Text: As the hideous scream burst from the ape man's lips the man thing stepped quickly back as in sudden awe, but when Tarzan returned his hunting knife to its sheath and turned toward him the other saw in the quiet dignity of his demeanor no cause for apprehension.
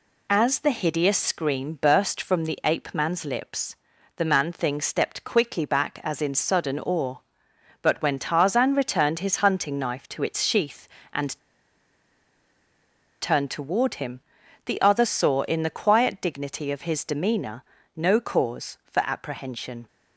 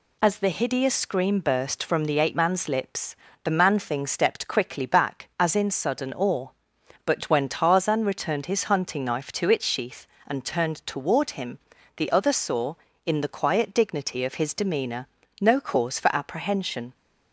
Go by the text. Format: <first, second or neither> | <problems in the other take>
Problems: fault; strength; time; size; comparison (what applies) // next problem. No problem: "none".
second | pauses between "lips" and "the"; at 3.7 s; 0.40 s long; slight in the second // pauses between "and" and "turned"; strong; at 11.3 s; 1.8 s long // pauses between "him" and "the"; at 14.2 s; 0.44 s long; also in the second // pauses between "demeanor" and "no"; slight; at 17.6 s; 0.32 s long; slight in the second